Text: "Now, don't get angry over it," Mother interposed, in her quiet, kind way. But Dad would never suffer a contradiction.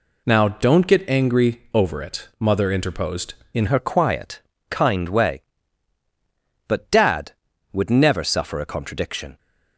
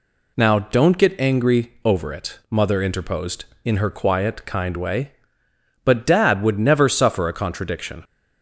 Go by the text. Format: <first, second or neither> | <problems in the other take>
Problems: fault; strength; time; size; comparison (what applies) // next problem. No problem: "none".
second | changes voice at "her"; from 3.6 s on; 5.7 s long